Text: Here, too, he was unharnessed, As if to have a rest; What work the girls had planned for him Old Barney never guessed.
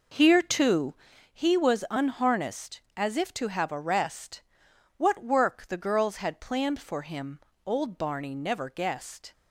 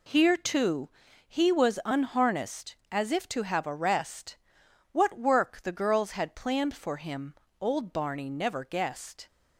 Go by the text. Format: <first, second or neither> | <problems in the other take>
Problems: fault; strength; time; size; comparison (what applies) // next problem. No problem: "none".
second | starts louder than the rest; noticeable; until 1.3 s; 5 dB // pauses between "him" and "Old"; slight; at 7.4 s; 0.24 s long; slight in the second